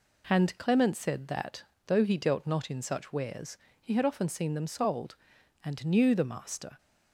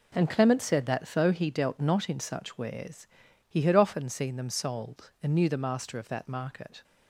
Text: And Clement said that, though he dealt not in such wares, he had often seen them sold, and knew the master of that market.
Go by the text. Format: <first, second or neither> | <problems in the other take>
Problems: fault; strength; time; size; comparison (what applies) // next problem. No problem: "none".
second | stops before "of that market"; at 6.7 s